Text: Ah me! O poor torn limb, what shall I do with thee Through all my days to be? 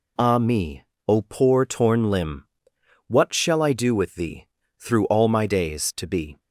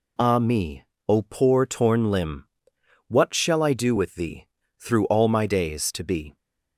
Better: neither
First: pauses between "thee" and "Through"; slight; at 4.4 s; 0.34 s long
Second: pauses between "thee" and "Through"; slight; at 4.4 s; 0.34 s long

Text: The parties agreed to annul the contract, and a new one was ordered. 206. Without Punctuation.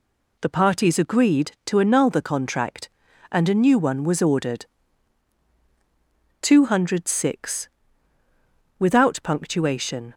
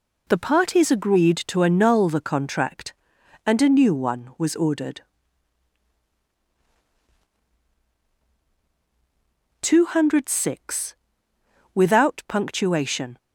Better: neither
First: none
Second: none

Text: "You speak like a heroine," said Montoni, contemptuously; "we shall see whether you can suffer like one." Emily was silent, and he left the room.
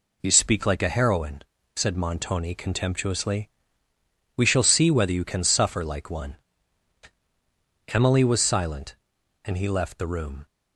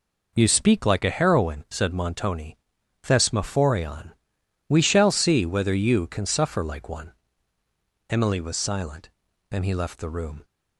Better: first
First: none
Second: says "thesmophorion" for "contemptuously"; at 3.0 s

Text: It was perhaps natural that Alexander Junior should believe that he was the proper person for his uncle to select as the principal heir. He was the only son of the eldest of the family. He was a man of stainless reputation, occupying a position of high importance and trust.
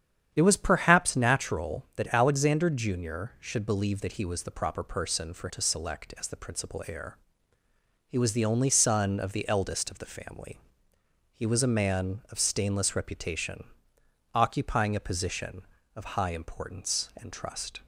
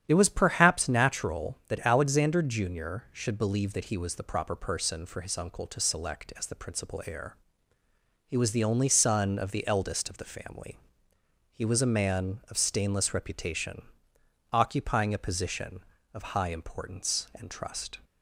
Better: second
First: starts louder than the rest; strong; until 1.3 s; 9 dB // skips "his uncle"; at 5.4 s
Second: starts louder than the rest; strong; until 1.0 s; 9 dB

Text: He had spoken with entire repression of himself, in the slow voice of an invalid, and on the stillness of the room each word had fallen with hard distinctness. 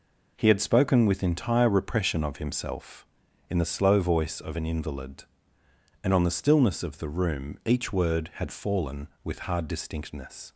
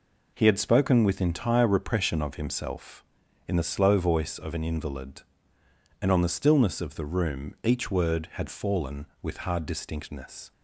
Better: neither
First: none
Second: none

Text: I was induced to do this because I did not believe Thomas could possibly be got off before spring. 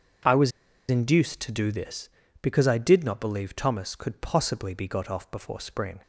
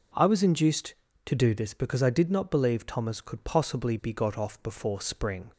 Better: second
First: pauses between "was" and "induced"; at 0.5 s; 0.40 s long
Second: none

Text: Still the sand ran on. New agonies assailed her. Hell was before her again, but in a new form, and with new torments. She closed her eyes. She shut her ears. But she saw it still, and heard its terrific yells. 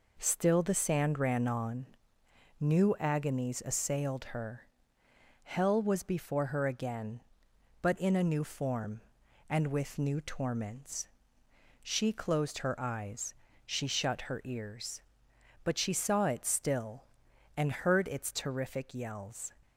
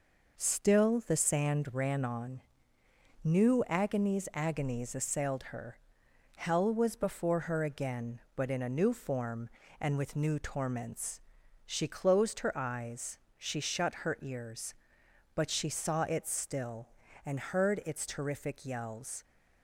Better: first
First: none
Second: says "agonies" twice; at 4.3 s

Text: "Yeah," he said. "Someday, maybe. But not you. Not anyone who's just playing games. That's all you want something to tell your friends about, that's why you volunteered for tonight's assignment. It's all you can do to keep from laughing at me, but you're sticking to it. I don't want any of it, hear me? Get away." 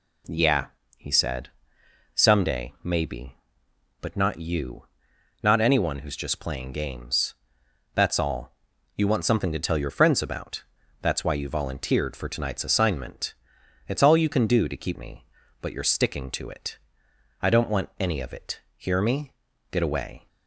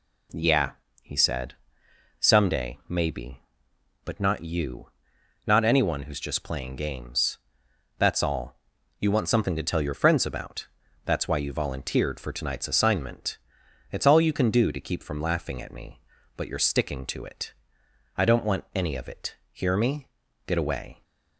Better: second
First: pauses between "all" and "you"; at 8.5 s; 0.42 s long // skips "from laughing at"; at 14.9 s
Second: pauses between "all" and "you"; at 8.5 s; 0.42 s long

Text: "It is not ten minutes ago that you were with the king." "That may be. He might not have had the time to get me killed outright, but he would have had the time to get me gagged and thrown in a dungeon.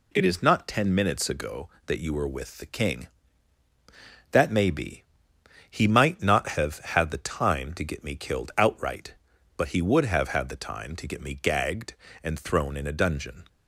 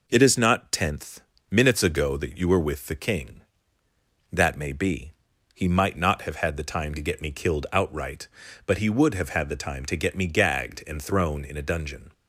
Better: first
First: none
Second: says "tenth" for "ten"; at 0.7 s

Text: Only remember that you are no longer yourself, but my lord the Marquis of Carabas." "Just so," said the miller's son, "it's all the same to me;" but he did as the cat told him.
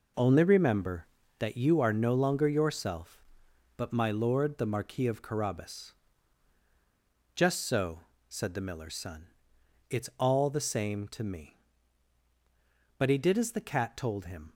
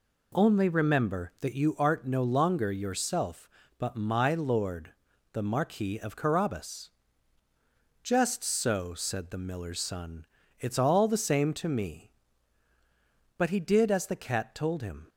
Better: first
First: none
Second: says "art" for "are"; at 1.7 s // pauses between "lord" and "the"; at 4.9 s; 0.42 s long

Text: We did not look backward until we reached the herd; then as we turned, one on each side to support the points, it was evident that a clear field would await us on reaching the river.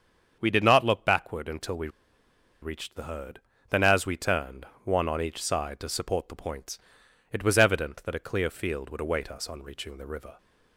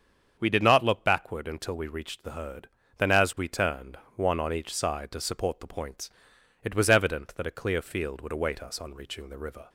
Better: second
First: starts louder than the rest; strong; until 1.4 s; 7.5 dB // pauses between "we" and "reached"; noticeable; at 1.8 s; 0.74 s long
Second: starts louder than the rest; strong; until 1.4 s; 7.5 dB

